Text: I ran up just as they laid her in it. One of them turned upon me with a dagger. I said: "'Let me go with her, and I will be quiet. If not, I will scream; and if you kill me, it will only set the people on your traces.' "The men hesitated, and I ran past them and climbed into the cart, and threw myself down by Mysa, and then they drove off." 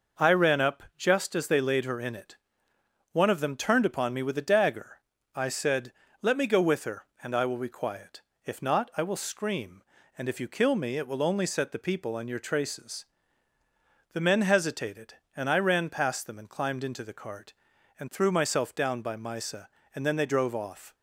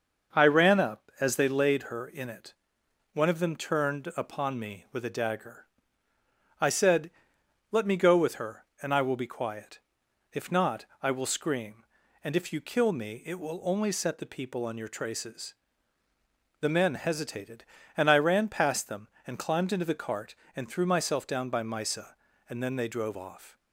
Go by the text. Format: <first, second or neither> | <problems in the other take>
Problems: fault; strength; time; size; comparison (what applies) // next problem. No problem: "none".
first | starts louder than the rest; noticeable; until 1.4 s; 6 dB // skips "just"; at 1.1 s